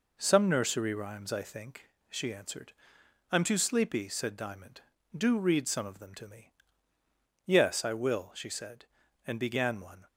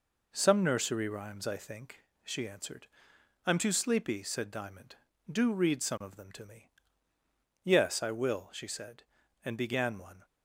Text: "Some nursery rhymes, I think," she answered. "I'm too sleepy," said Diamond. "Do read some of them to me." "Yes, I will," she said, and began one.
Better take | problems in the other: neither | none

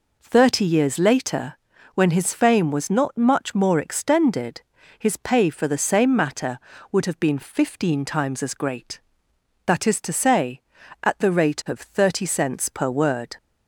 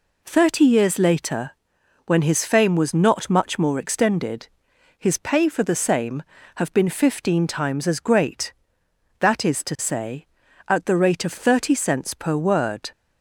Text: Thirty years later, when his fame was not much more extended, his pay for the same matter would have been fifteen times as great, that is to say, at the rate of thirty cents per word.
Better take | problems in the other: first | skips "matter would"; at 6.3 s

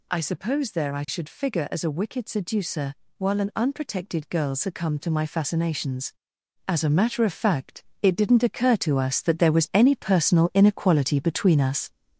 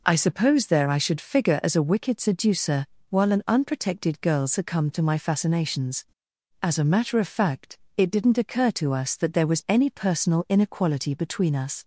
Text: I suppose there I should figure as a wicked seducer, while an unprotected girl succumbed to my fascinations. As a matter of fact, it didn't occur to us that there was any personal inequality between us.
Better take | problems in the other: second | gets louder; noticeable; throughout; 4.5 dB

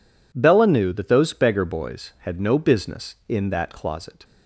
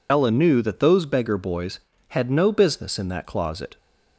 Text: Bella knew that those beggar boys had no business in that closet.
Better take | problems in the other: first | loses the start of "Bella"; at 0.0 s; 65 ms

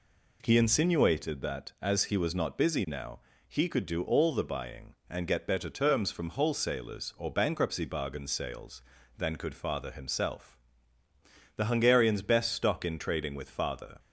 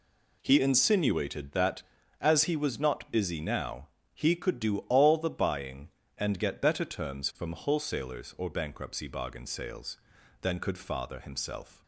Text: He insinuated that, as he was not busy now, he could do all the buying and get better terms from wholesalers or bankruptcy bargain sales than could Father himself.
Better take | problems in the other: second | goes on to say "The Hungarian's best stock in trading with Father"; strong; from 11.5 s on; 2.4 s long

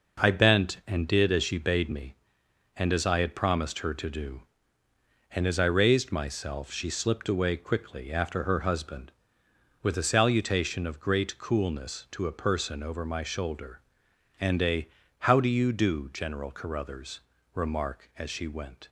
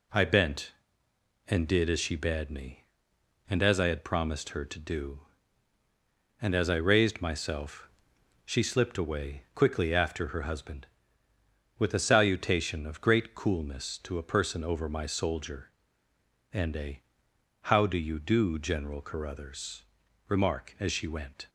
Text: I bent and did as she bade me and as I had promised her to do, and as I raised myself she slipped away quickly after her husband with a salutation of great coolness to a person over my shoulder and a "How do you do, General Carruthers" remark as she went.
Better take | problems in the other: first | pauses between "myself" and "she"; noticeable; at 7.8 s; 0.56 s long // says "soldier" for "shoulder"; at 15.0 s // pauses between "a" and "How"; noticeable; at 17.0 s; 0.62 s long; slight in the first // pauses between "Carruthers" and "remark"; at 19.8 s; 0.44 s long; slight in the first

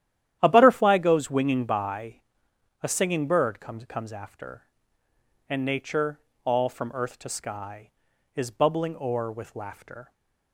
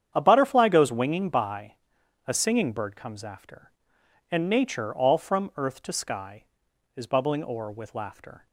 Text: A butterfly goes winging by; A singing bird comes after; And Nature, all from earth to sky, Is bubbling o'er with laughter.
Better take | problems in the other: second | starts louder than the rest; strong; until 1.4 s; 11.5 dB; strong in the second // says "comes" twice; at 3.8 s

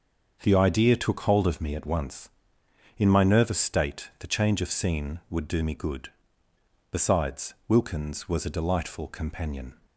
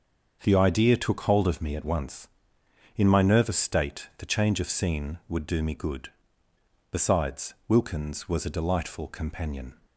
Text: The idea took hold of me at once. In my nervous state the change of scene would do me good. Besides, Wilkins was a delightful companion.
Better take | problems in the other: neither | starts louder than the rest; the same in both

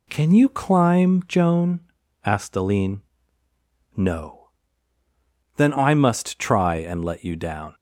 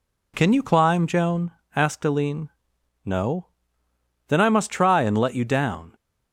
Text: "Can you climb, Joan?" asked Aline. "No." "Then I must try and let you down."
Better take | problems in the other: neither | none

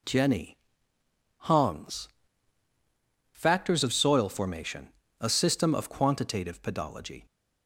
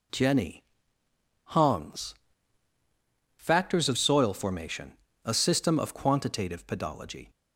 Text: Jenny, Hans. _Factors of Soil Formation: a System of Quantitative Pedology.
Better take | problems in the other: neither | none

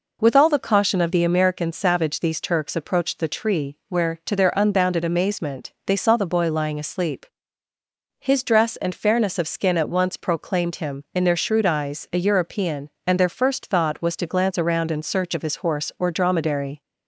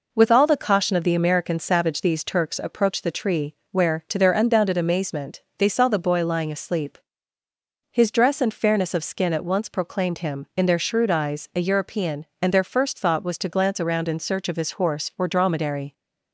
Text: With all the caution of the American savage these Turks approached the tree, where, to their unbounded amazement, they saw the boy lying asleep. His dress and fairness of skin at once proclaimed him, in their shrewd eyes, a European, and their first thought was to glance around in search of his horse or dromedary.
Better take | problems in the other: neither | none

